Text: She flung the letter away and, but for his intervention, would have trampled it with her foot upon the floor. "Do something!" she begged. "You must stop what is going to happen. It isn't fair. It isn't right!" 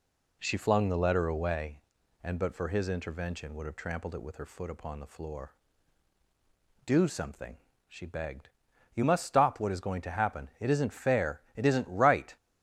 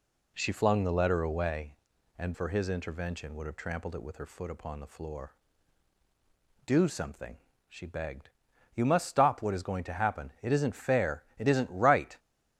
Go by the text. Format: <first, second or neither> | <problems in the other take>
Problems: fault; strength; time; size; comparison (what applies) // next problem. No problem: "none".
first | skips "but"; at 2.3 s